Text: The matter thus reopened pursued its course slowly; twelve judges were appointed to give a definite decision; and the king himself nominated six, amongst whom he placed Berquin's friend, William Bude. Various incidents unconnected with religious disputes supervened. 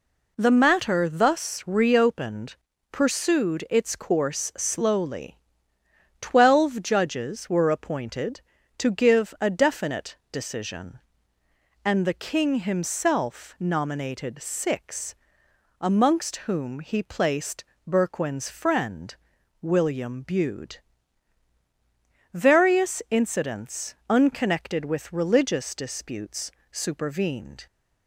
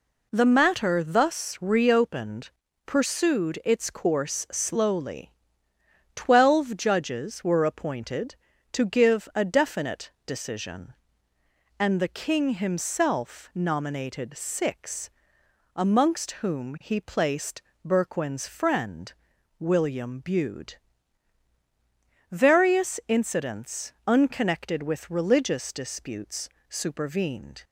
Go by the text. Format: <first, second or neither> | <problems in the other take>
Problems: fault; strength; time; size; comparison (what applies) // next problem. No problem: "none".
neither | pauses between "reopened" and "pursued"; slight; the same in both // pauses between "placed" and "Berquin's"; slight; the same in both // pauses between "disputes" and "supervened"; slight; the same in both